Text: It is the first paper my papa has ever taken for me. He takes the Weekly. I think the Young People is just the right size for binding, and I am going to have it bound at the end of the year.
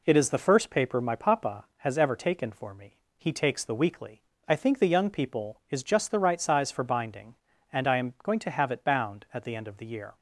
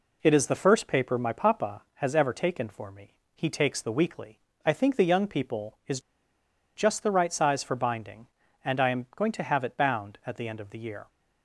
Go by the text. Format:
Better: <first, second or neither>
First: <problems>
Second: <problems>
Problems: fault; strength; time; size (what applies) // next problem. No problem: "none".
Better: first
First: none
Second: pauses between "is" and "just"; noticeable; at 6.0 s; 0.74 s long